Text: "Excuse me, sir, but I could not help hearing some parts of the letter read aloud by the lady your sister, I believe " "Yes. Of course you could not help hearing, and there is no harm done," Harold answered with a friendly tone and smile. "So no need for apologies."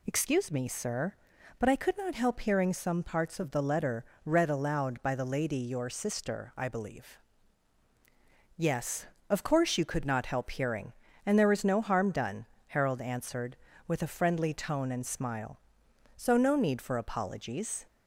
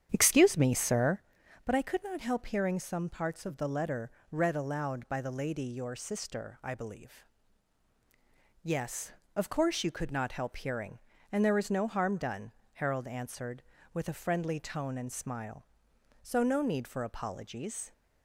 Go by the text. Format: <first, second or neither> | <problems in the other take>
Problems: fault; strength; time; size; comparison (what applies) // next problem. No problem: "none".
first | starts louder than the rest; strong; until 1.2 s; 9.5 dB // pauses between "letter" and "read"; slight; at 4.1 s; 0.20 s long; slight in the first